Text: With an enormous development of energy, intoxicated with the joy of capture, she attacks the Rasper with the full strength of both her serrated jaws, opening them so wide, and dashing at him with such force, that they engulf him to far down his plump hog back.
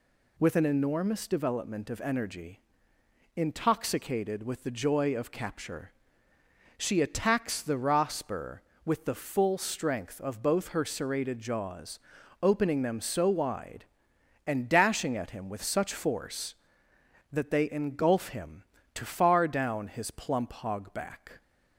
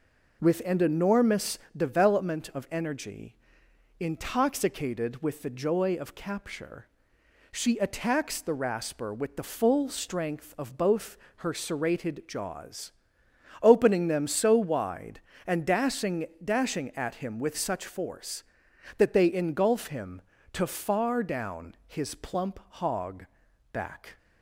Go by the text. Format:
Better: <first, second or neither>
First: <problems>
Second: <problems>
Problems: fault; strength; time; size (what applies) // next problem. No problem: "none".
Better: first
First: none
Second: pauses between "enormous" and "development"; slight; at 1.5 s; 0.18 s long // pauses between "both" and "her"; slight; at 11.1 s; 0.18 s long // says "dashing" twice; at 16.4 s // pauses between "hog" and "back"; noticeable; at 23.2 s; 0.46 s long